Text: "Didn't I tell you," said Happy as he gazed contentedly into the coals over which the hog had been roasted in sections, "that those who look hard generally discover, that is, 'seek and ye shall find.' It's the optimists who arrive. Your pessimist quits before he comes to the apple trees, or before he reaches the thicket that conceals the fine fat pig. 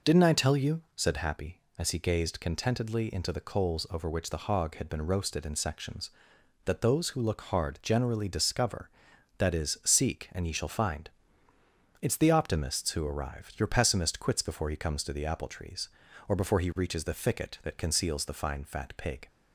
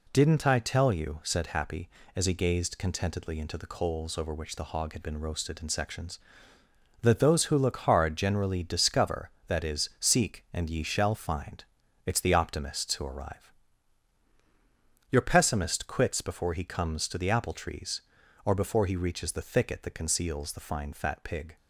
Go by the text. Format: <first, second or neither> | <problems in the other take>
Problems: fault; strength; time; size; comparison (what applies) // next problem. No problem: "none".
neither | none